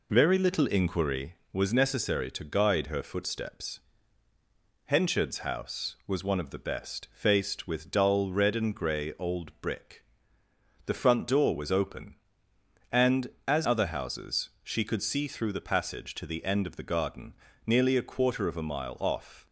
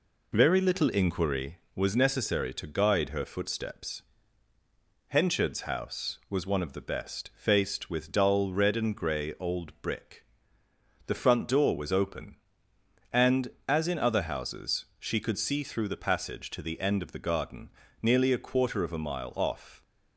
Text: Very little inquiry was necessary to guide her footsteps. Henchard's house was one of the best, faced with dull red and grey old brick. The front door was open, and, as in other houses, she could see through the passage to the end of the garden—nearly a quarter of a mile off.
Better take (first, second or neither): second